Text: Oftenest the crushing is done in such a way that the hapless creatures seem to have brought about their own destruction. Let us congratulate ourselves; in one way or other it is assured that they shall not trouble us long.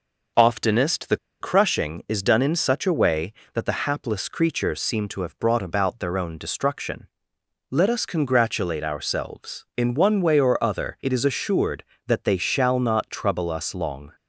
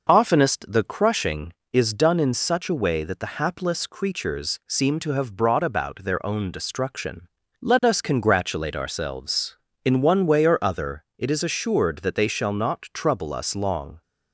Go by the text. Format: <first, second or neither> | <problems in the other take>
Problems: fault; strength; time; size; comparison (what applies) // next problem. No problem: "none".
second | pauses between "the" and "crushing"; slight; at 1.1 s; 0.23 s long